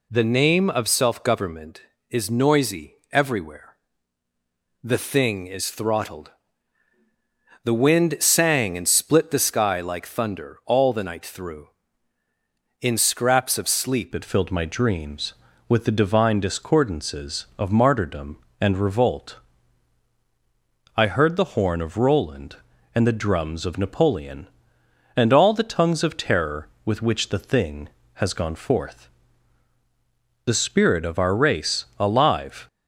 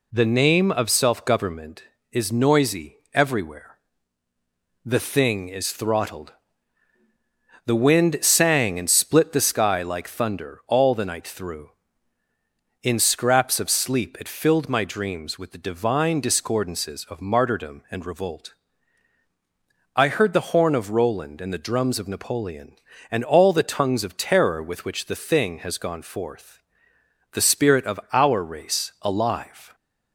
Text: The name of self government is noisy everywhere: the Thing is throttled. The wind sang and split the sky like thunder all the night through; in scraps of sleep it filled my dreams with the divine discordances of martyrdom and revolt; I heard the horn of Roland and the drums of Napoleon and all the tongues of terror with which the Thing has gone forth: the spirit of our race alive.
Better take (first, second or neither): second